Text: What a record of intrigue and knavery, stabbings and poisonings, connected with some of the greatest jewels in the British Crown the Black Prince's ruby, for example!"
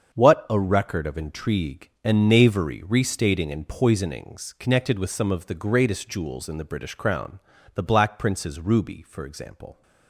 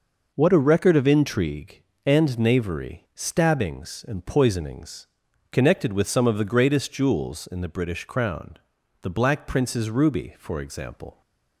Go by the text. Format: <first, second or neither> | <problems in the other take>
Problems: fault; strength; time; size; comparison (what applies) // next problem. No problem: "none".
second | starts louder than the rest; until 1.2 s; 7 dB // says "restating" for "stabbings"; at 2.8 s // pauses between "Crown" and "the"; slight; at 7.3 s; 0.36 s long; also in the second